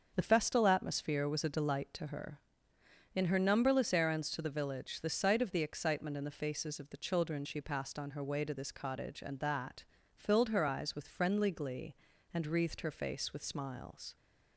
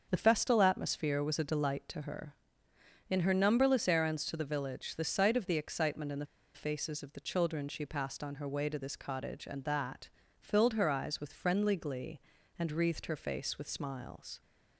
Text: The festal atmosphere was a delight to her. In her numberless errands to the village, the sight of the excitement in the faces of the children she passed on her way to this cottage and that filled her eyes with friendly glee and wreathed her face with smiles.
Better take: first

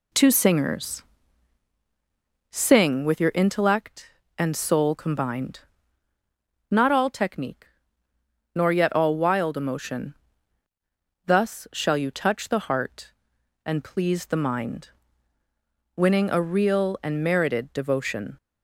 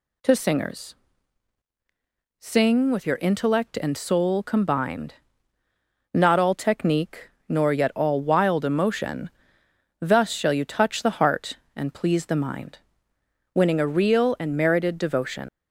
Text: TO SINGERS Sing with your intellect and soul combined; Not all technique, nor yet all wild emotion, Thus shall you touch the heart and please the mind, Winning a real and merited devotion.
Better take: first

